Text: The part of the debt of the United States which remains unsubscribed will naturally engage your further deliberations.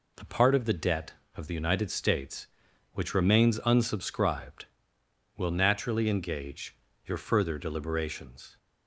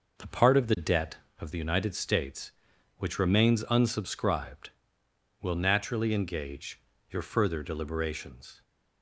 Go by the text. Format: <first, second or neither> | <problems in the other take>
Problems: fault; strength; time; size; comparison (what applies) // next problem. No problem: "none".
first | starts louder than the rest; noticeable; until 1.5 s; 5.5 dB // pauses between "engage" and "your"; slight; at 6.7 s; 0.30 s long; slight in the first